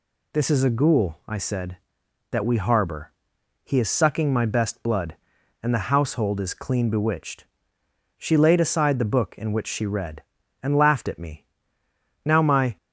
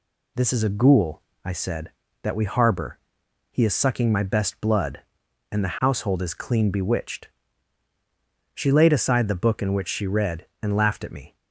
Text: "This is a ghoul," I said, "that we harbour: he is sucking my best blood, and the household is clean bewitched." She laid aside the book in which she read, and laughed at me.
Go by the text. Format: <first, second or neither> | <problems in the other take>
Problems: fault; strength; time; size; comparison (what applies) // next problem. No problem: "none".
second | goes on to say "Now my"; from 12.2 s on; 0.52 s long